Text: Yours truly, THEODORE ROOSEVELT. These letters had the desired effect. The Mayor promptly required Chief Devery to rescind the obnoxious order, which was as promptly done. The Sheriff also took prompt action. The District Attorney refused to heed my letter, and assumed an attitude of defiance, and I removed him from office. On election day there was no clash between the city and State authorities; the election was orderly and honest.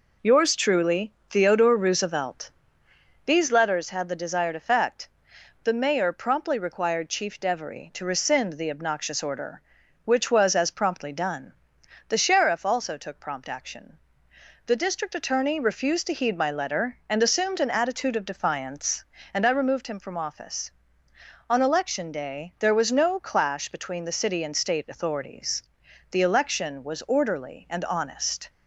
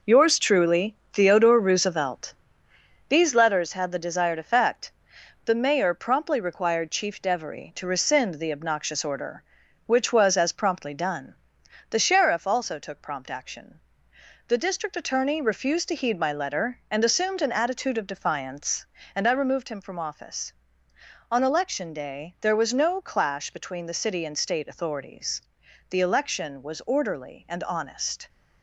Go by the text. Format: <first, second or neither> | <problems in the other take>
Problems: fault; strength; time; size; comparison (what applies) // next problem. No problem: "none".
first | gets quieter; noticeable; throughout; 6 dB